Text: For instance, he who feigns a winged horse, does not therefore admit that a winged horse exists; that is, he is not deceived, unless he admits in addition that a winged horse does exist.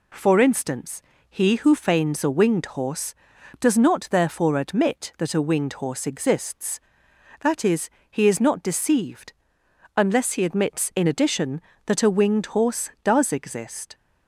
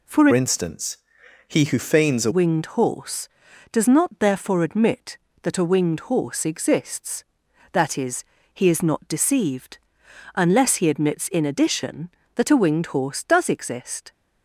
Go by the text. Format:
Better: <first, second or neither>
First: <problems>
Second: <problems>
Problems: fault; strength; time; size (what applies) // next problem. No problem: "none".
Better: first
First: none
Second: changes voice from "instance" to "a"; from 0.3 to 2.3 s; 2.0 s long